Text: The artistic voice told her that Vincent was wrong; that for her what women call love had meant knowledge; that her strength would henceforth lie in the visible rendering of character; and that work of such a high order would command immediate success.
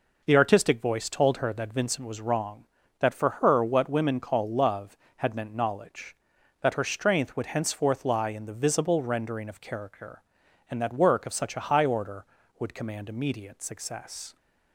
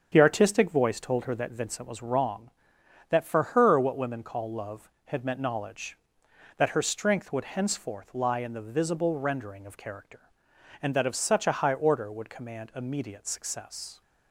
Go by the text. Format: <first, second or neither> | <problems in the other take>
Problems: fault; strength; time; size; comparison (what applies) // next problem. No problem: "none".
first | starts louder than the rest; strong; until 1.1 s; 7.5 dB // pauses between "for" and "her"; slight; at 3.4 s; 0.16 s long // skips "work"; at 11.0 s